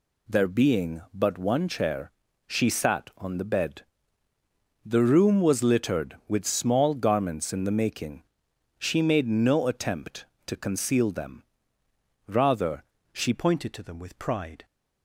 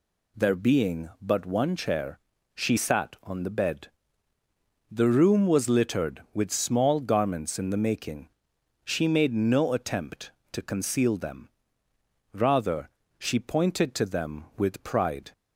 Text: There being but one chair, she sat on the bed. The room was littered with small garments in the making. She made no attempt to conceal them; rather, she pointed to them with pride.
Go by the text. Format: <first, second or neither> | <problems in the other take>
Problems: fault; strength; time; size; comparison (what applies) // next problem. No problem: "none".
second | changes voice at "pointed"; from 13.3 s on; 1.3 s long